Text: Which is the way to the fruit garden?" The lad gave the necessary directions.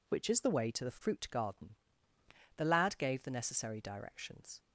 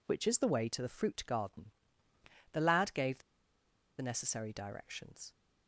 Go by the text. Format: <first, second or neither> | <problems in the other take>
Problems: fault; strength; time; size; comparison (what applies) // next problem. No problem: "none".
first | pauses between "the" and "necessary"; noticeable; at 3.2 s; 0.79 s long